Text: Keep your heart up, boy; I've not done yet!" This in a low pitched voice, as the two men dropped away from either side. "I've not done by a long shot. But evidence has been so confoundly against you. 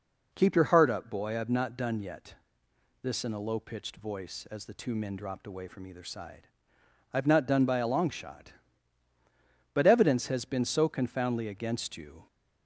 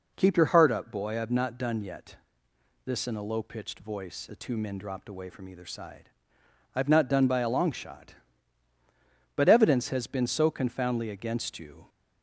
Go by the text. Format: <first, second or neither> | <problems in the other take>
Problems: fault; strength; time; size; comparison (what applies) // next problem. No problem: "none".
first | skips "as"; at 4.2 s